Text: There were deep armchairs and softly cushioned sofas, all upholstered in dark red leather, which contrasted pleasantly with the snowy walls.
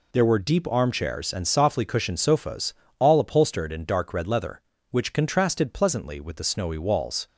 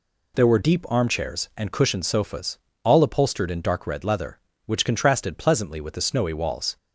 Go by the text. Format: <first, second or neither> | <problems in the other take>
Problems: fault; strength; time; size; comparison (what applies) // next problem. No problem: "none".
first | skips "softly"; at 1.7 s